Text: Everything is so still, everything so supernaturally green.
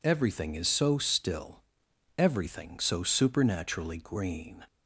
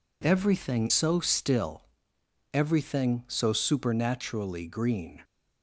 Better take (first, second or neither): first